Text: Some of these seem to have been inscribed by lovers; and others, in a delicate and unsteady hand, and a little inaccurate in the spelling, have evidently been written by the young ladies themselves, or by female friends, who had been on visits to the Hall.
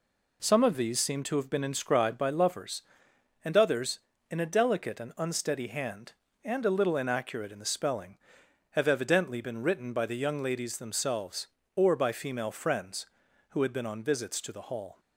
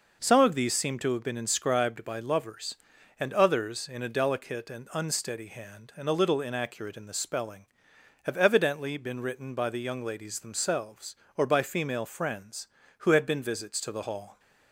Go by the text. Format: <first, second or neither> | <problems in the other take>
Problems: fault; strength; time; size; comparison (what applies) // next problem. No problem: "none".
first | skips "on"; at 13.4 s